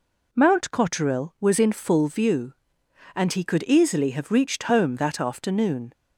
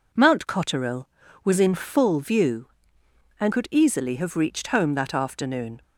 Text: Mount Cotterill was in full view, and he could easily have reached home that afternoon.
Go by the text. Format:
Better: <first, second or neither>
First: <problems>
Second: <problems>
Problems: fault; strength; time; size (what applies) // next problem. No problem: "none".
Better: first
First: none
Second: skips "he"; at 3.5 s